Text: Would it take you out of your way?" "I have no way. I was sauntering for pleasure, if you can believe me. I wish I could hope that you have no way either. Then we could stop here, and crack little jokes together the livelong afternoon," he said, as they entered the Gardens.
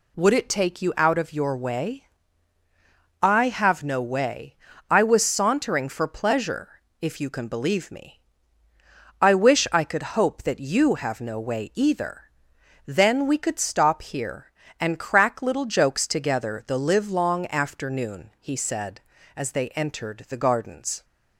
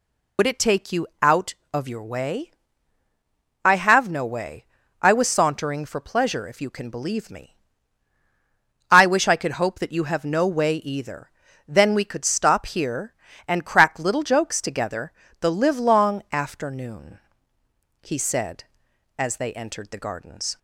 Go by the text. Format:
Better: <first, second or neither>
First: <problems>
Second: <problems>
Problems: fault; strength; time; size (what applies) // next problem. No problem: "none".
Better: first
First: none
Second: loses the start of "Would"; at 0.3 s; 70 ms // pauses between "together" and "the"; slight; at 15.1 s; 0.28 s long